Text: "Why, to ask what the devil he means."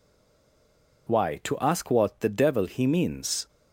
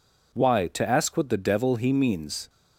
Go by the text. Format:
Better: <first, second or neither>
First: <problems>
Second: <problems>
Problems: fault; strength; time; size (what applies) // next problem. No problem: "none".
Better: second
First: stays silent before the first word; until 1.0 s; 1.0 s long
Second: none